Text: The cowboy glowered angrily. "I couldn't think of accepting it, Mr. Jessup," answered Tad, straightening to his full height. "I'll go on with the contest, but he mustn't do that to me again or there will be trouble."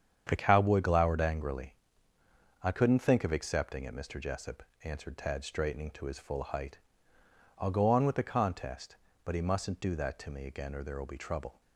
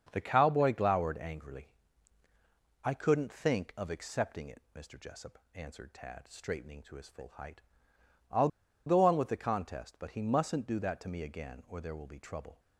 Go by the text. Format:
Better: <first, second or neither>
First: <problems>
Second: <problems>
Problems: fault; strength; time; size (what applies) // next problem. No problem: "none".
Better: first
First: starts louder than the rest; strong; until 1.3 s; 8 dB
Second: starts louder than the rest; until 1.1 s; 7 dB // pauses between "I'll" and "go"; at 8.4 s; 0.38 s long